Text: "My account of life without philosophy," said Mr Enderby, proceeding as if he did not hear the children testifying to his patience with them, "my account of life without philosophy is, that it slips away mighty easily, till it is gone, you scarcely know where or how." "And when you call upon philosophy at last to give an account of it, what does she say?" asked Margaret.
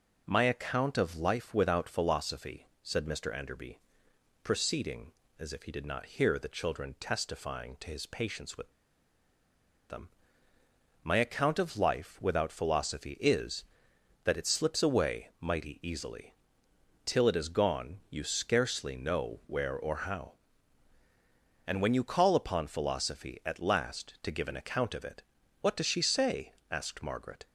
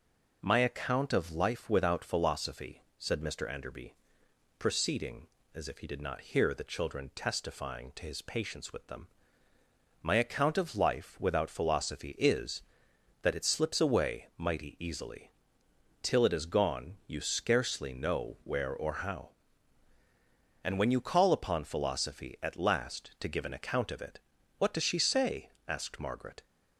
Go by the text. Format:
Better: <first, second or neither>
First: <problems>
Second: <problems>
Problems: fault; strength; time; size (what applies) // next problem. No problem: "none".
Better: second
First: pauses between "with" and "them"; at 8.7 s; 1.1 s long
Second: none